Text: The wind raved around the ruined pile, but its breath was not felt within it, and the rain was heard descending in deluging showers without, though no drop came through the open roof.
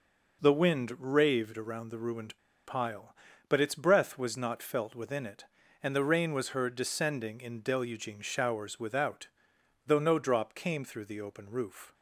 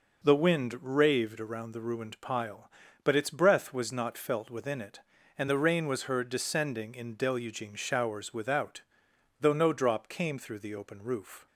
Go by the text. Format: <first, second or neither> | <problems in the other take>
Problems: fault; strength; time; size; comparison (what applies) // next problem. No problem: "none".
second | pauses between "ruined" and "pile"; slight; at 2.3 s; 0.28 s long